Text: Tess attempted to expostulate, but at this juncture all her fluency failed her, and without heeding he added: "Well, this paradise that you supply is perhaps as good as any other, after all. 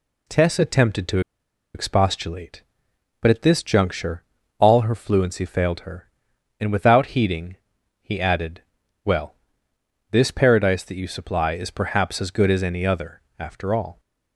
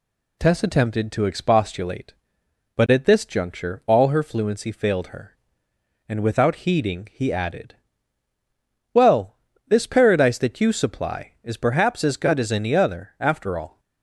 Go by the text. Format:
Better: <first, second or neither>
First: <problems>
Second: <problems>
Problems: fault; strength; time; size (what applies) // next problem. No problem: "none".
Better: second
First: pauses between "to" and "expostulate"; noticeable; at 1.1 s; 0.55 s long // pauses between "juncture" and "all"; slight; at 4.2 s; 0.36 s long // pauses between "heeding" and "he"; at 7.5 s; 0.44 s long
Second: none